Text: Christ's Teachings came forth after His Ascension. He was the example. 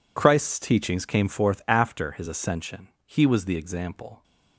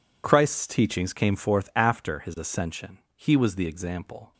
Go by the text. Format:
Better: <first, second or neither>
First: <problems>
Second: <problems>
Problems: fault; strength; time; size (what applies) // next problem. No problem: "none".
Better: neither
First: none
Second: none